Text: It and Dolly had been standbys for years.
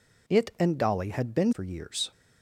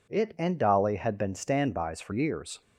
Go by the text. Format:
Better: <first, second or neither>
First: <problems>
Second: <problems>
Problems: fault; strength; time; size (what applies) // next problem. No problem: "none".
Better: second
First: skips "standbys"; at 1.5 s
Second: none